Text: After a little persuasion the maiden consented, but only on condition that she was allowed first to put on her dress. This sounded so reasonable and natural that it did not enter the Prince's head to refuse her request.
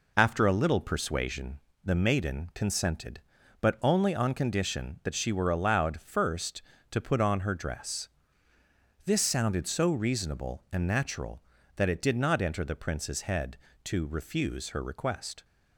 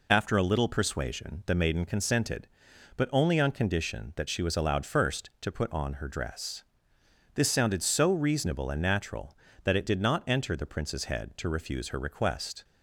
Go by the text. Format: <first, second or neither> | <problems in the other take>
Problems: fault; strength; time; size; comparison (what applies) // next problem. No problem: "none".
second | pauses between "persuasion" and "the"; slight; at 1.5 s; 0.26 s long // says "were" for "was"; at 5.3 s